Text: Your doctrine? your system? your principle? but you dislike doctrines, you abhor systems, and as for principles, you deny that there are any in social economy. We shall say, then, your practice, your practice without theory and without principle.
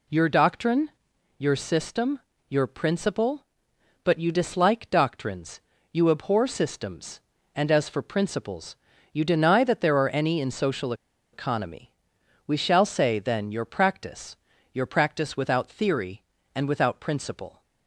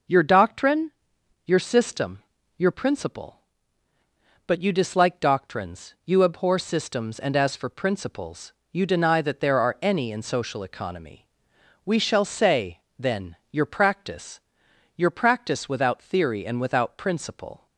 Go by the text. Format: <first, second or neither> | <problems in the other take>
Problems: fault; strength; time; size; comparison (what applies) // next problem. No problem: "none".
second | pauses between "social" and "economy"; at 10.9 s; 0.39 s long